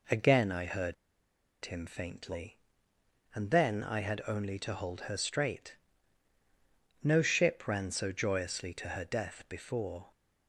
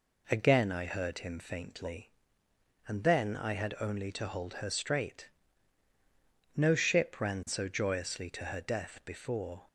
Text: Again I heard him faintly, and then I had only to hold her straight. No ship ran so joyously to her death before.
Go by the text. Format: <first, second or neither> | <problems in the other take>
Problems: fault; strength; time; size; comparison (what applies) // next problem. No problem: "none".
second | pauses between "heard" and "him"; noticeable; at 0.9 s; 0.69 s long